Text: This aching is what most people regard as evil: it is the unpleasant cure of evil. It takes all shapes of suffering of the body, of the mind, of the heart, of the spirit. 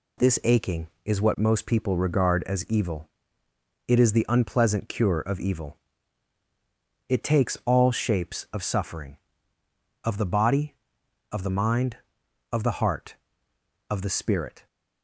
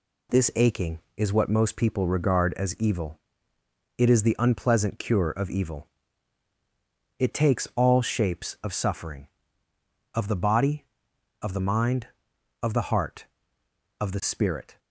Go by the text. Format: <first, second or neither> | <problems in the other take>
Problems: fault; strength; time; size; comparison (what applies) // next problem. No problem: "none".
neither | none